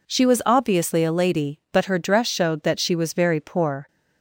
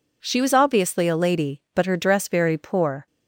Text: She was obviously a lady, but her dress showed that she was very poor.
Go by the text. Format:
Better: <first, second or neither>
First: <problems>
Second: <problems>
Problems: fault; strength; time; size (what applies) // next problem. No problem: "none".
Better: first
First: none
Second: skips "showed that she was"; at 2.2 s